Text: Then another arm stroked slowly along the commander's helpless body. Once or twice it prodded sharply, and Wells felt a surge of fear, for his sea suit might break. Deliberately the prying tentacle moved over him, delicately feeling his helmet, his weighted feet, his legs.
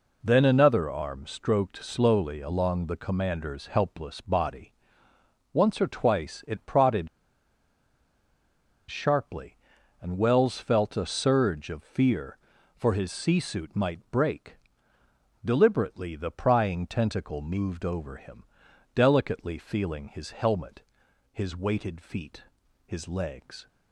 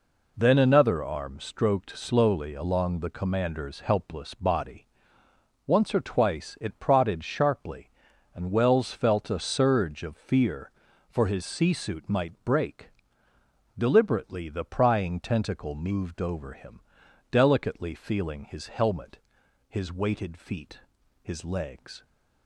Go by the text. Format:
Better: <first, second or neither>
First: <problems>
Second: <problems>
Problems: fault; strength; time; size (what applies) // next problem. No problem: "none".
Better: second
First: pauses between "prodded" and "sharply"; strong; at 7.0 s; 1.8 s long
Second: none